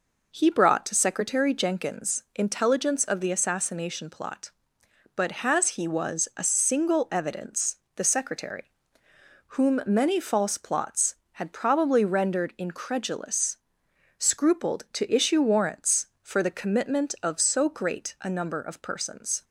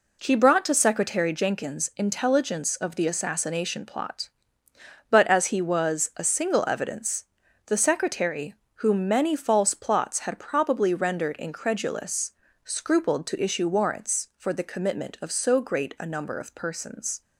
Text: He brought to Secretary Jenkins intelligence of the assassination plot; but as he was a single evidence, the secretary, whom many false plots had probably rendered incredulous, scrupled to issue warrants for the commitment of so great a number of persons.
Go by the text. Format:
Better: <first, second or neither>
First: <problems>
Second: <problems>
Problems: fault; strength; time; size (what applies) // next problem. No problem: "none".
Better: second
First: says "has" for "as"; at 5.4 s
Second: none